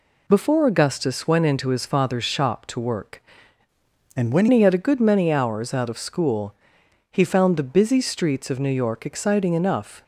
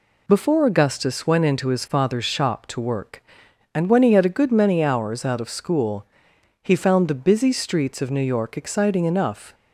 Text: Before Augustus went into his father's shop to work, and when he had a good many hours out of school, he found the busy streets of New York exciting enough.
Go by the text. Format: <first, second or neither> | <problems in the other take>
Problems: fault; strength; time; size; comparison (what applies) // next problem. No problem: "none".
second | changes voice from "and" to "when"; from 4.1 to 4.4 s; 0.3 s long